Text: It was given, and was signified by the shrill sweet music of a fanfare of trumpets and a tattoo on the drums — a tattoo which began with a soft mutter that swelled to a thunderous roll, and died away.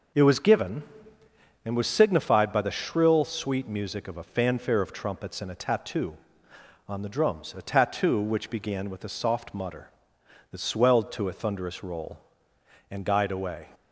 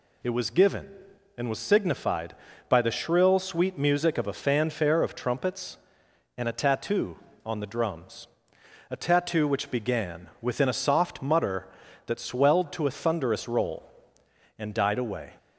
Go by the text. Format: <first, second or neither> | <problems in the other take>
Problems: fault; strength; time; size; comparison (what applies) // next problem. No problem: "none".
first | says "within" for "with"; at 10.4 s